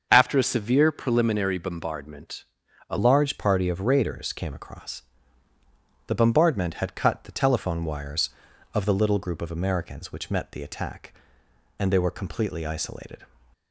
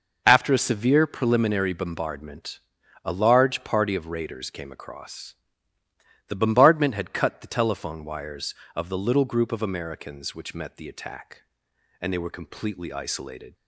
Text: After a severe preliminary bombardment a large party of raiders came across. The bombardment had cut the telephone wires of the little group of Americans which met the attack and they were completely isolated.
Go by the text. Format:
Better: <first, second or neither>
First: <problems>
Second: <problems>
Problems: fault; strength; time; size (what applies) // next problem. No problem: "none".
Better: second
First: starts louder than the rest; until 1.1 s; 6.5 dB // pauses between "bombardment" and "a"; at 2.4 s; 0.44 s long // changes voice at "large"; from 2.9 s on; 10.3 s long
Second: pauses between "bombardment" and "a"; at 2.5 s; 0.44 s long